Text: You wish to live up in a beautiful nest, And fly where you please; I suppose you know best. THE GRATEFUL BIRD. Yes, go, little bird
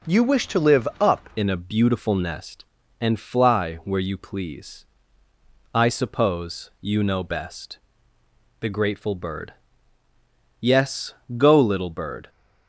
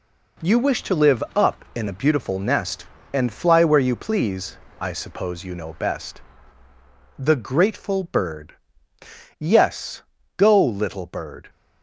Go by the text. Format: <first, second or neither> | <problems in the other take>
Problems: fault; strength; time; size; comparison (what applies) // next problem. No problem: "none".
second | changes voice at "in"; from 1.3 s on; 10.9 s long